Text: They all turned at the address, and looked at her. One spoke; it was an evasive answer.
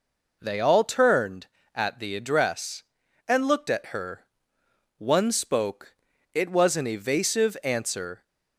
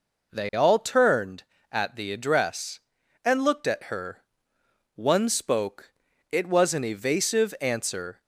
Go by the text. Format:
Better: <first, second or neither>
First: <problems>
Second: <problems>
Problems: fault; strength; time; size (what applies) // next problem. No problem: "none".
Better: neither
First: none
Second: none